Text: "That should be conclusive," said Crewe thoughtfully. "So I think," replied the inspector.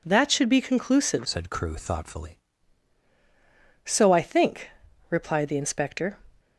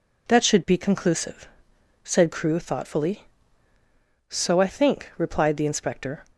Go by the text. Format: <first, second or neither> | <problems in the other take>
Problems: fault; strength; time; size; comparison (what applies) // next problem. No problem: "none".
second | changes voice from "said" to "thoughtfully"; from 1.2 to 2.4 s; 1.2 s long